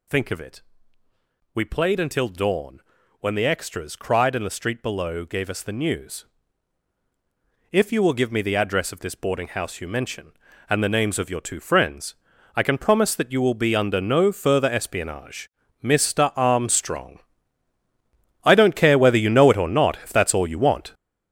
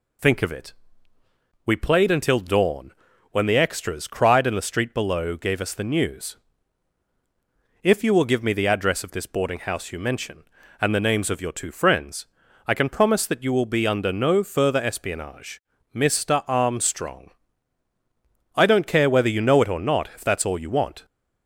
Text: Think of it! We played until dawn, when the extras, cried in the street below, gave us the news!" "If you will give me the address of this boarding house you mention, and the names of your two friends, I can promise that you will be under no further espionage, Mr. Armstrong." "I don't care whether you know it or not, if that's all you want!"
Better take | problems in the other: second | gets louder; strong; throughout; 9.5 dB

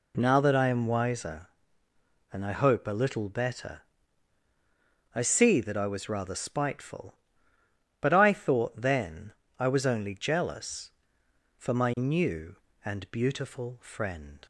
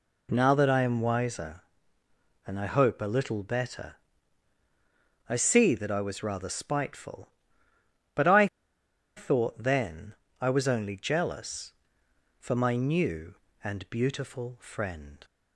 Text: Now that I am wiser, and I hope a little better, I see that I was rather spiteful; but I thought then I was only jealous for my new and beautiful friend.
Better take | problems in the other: first | pauses between "I" and "thought"; noticeable; at 8.4 s; 0.70 s long // pauses between "then" and "I"; slight; at 10.1 s; 0.28 s long; slight in the first

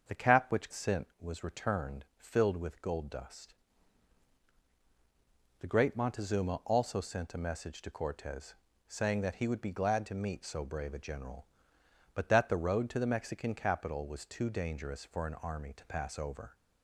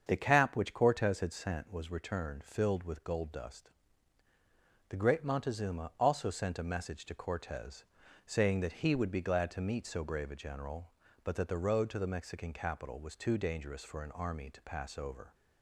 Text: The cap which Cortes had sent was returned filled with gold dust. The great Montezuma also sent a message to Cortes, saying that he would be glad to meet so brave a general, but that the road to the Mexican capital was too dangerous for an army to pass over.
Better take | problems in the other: second | starts louder than the rest; until 1.2 s; 6.5 dB; strong in the second // skips "Cortes had"; at 0.7 s

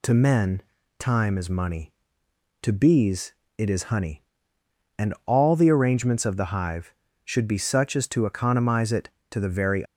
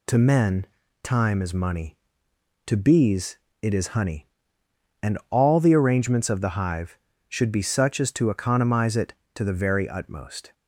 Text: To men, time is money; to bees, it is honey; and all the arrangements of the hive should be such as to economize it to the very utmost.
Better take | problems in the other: second | stops before "utmost"; at 9.8 s

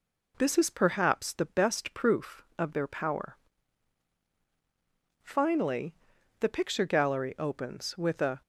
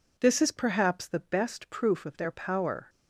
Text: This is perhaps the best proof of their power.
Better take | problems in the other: second | goes on to say "Finally the picture gallery opens with a"; strong; from 5.2 s on; 3.1 s long

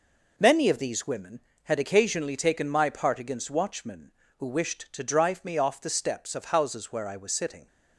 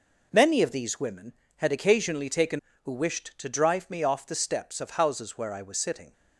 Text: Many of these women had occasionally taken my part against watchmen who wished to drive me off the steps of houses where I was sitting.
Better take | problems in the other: first | skips "my part against watchmen"; at 2.7 s

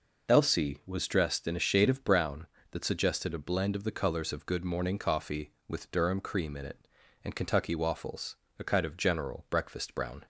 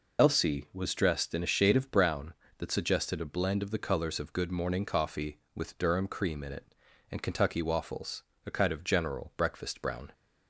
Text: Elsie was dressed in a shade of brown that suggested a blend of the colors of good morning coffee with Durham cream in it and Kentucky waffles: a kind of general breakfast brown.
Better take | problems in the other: first | loses the start of "Elsie"; at 0.1 s; 40 ms

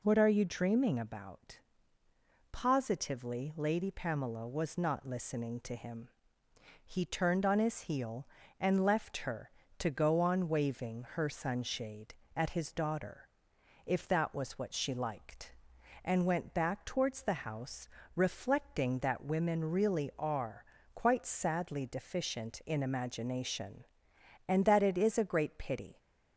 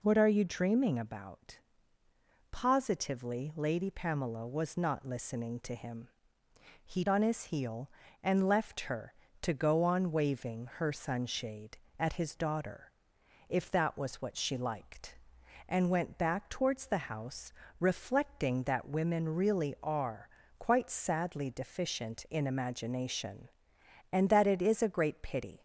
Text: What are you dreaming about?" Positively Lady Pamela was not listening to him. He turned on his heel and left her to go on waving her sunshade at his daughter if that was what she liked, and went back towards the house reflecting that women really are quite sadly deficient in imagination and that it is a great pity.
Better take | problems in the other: first | skips "turned"; at 7.0 s // pauses between "daughter" and "if"; noticeable; at 12.9 s; 0.58 s long; noticeable in the first // pauses between "house" and "reflecting"; slight; at 17.5 s; 0.28 s long; slight in the first // pauses between "are" and "quite"; slight; at 20.2 s; 0.32 s long; slight in the first

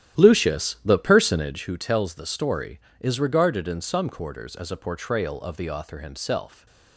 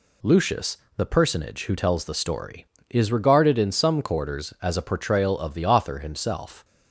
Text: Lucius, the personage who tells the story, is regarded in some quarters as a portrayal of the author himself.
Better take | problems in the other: second | starts louder than the rest; strong; until 1.7 s; 12 dB // stays silent after the last word; slight; from 6.4 s on; 0.5 s long

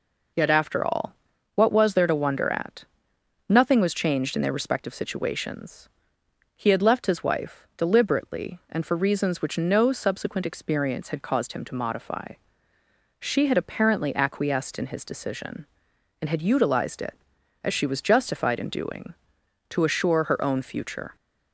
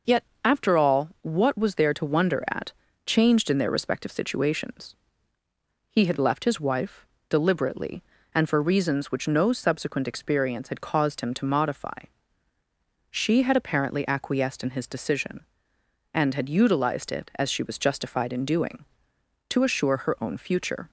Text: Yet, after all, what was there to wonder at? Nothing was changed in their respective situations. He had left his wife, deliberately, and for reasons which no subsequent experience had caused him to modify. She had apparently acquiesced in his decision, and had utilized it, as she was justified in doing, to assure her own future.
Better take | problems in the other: first | skips "Nothing was"; at 2.8 s

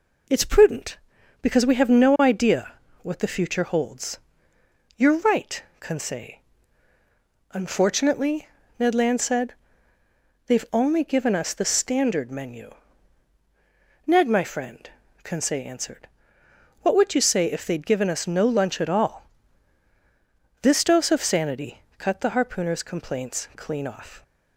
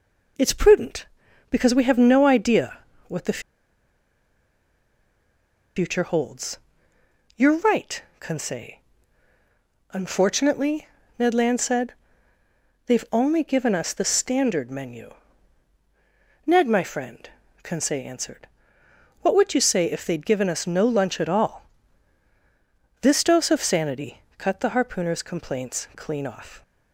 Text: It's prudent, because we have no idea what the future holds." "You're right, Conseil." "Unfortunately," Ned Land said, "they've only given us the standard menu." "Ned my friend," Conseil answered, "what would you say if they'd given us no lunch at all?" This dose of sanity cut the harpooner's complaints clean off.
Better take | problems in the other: first | pauses between "idea" and "what"; slight; at 2.7 s; 0.30 s long; slight in the first // pauses between "the" and "future"; strong; at 3.3 s; 2.3 s long // pauses between "sanity" and "cut"; slight; at 24.1 s; 0.18 s long; slight in the first

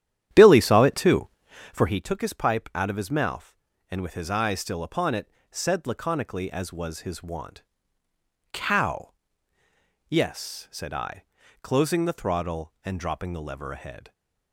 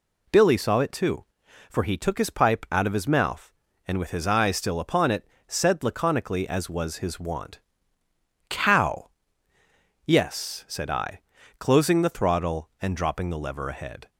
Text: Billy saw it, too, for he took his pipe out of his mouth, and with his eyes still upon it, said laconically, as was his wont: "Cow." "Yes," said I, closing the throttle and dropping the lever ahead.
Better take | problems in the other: second | starts louder than the rest; strong; until 2.1 s; 11 dB

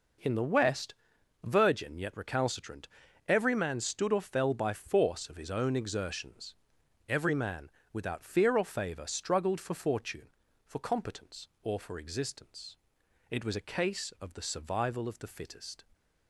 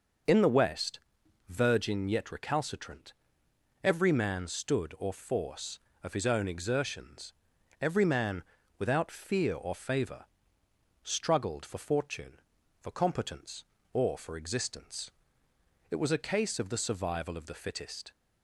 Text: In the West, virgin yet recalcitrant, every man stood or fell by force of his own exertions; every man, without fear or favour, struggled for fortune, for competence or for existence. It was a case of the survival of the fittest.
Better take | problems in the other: first | skips "fell by"; at 5.1 s

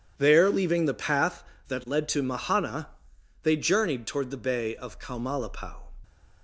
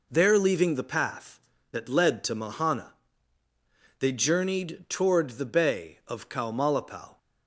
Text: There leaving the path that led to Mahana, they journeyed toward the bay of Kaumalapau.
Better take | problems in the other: neither | none

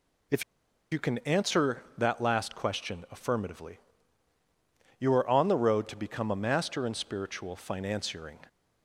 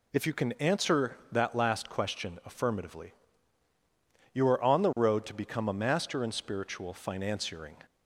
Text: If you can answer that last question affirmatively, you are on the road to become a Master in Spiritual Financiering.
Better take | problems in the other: second | pauses between "If" and "you"; noticeable; at 0.4 s; 0.49 s long

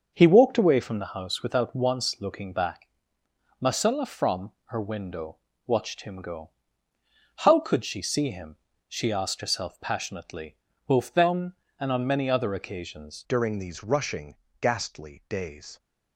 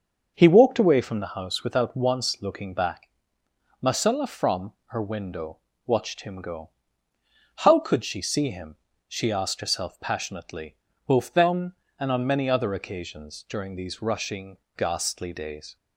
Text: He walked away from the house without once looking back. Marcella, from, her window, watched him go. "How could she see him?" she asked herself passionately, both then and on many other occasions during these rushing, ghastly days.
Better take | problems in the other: second | starts louder than the rest; until 1.1 s; 6.5 dB; also in the second // changes voice at "during"; from 13.2 s on; 2.5 s long

